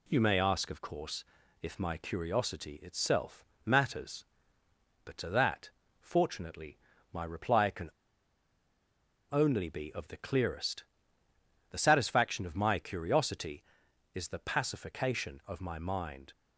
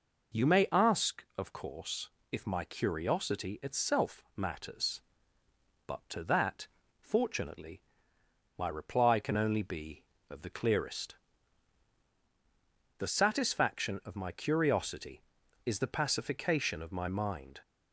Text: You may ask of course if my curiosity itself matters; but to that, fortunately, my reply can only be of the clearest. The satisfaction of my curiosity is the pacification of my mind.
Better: second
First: pauses between "course" and "if"; slight; at 1.2 s; 0.36 s long // pauses between "itself" and "matters"; slight; at 3.4 s; 0.22 s long // pauses between "can" and "only"; strong; at 7.8 s; 1.3 s long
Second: pauses between "course" and "if"; slight; at 2.0 s; 0.22 s long

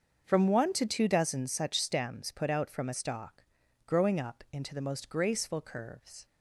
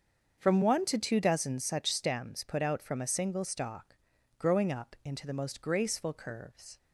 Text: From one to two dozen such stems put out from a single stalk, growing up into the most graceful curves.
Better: second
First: starts louder than the rest; until 1.2 s; 6.5 dB // skips "single"; at 2.9 s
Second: starts louder than the rest; until 1.4 s; 7 dB

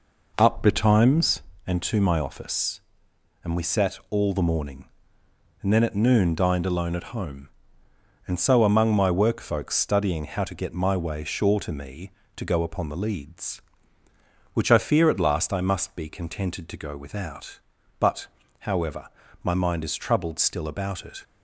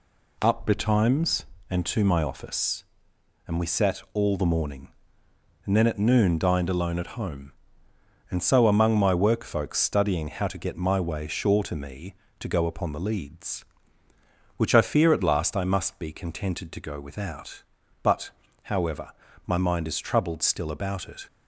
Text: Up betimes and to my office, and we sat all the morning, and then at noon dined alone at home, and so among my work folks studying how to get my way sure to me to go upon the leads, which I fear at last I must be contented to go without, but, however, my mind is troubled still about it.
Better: second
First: starts louder than the rest; noticeable; until 1.5 s; 5 dB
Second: none

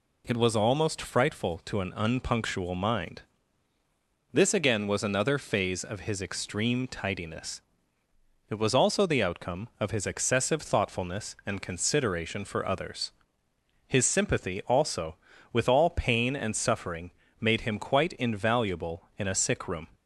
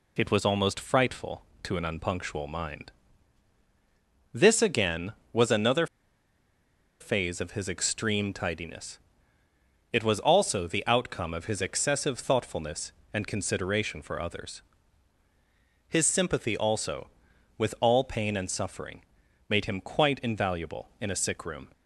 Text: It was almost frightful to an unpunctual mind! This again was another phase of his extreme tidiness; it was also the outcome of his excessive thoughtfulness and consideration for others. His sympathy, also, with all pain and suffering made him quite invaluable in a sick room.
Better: first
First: pauses between "suffering" and "made"; slight; at 17.1 s; 0.30 s long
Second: pauses between "another" and "phase"; at 5.8 s; 1.1 s long // pauses between "suffering" and "made"; noticeable; at 19.0 s; 0.46 s long

